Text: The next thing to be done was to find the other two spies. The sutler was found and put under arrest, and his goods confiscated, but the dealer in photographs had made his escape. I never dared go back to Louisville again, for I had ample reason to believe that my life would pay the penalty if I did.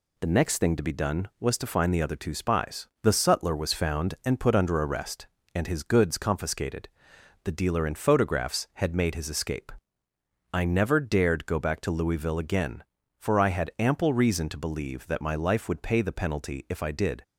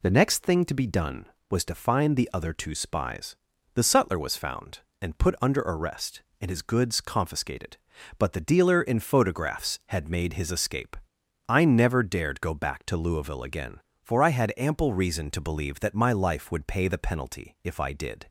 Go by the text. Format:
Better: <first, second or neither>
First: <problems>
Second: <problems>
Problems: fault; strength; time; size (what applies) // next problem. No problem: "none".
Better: second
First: skips "but"; at 7.1 s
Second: none